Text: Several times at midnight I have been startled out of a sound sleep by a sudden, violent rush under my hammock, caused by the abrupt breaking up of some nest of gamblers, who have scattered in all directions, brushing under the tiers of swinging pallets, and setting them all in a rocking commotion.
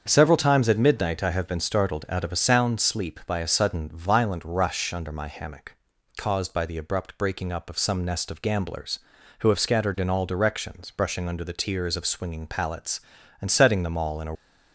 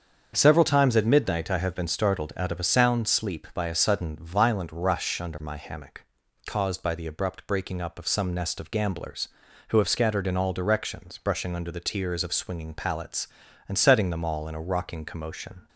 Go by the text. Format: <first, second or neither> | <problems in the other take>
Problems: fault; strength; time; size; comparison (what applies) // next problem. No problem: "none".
second | starts louder than the rest; until 1.0 s; 7 dB; also in the second // stops before "rocking commotion"; at 14.3 s